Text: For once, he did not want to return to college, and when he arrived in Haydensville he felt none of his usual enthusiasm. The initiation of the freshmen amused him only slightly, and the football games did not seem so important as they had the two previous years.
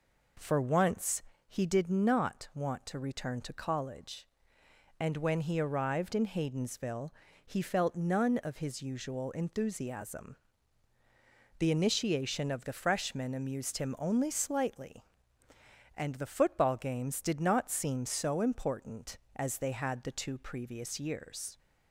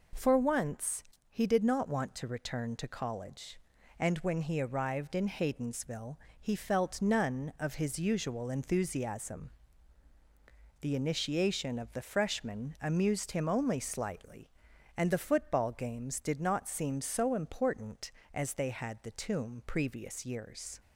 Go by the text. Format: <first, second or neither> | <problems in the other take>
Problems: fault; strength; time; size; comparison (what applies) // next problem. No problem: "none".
first | pauses between "Haydensville" and "he"; slight; at 6.1 s; 0.24 s long; slight in the first // says "tomb" for "two"; at 19.1 s